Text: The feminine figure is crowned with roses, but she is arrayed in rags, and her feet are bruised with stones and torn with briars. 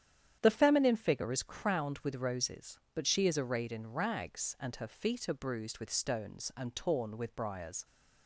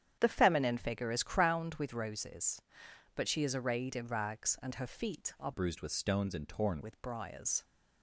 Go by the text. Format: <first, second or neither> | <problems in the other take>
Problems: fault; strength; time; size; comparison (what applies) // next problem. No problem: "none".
first | starts louder than the rest; strong; until 1.2 s; 9 dB; strong in the first // changes voice from "bruised" to "torn"; from 5.5 to 6.8 s; 1.3 s long